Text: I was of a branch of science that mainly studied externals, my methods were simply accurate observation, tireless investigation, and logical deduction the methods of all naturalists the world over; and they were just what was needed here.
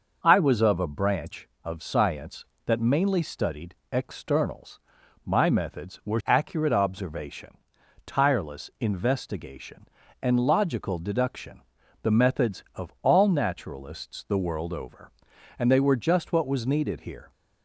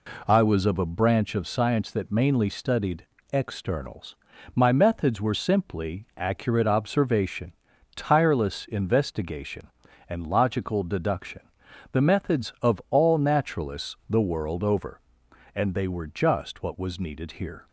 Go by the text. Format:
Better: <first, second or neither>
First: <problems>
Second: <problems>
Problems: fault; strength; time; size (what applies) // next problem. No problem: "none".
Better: second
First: pauses between "studied" and "externals"; slight; at 3.7 s; 0.18 s long // skips "simply"; at 6.2 s // pauses between "deduction" and "the"; at 11.6 s; 0.42 s long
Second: pauses between "studied" and "externals"; slight; at 3.0 s; 0.28 s long // pauses between "deduction" and "the"; noticeable; at 11.4 s; 0.50 s long